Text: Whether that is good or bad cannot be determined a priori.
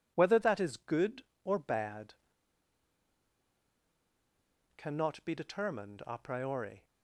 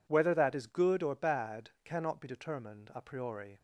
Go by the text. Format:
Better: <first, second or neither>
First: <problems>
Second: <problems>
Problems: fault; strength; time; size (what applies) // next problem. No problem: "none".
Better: second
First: pauses between "bad" and "cannot"; strong; at 2.1 s; 2.6 s long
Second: none